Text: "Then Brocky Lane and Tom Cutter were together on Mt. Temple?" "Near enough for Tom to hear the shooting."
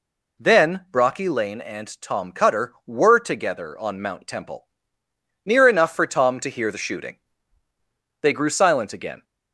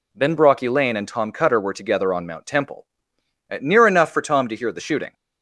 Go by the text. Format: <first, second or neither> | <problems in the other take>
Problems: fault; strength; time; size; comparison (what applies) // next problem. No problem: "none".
second | goes on to say "They grew silent again"; noticeable; from 8.2 s on; 1.0 s long